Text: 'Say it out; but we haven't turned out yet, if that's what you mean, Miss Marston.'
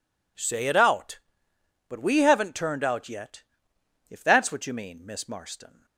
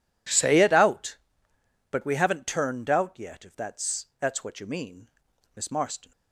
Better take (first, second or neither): first